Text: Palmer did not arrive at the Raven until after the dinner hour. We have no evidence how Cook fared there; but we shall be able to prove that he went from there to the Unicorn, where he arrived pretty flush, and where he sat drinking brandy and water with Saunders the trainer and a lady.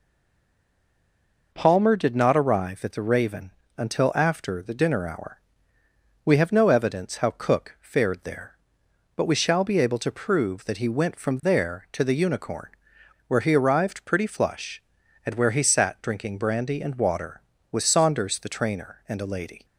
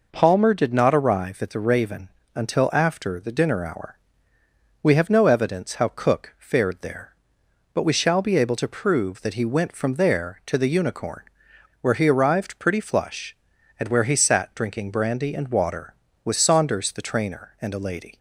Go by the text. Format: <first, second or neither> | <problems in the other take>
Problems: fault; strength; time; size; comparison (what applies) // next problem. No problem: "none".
second | stays silent before the first word; noticeable; until 1.5 s; 1.5 s long // pauses between "Raven" and "until"; slight; at 3.5 s; 0.24 s long; slight in the second